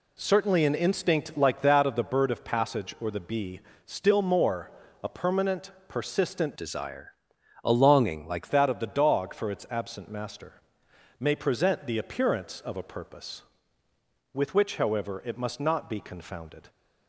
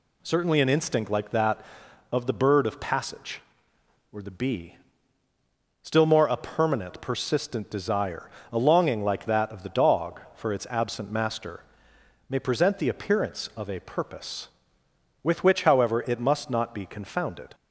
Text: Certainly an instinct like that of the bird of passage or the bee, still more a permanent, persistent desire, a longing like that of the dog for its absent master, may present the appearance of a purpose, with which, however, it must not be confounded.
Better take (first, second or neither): second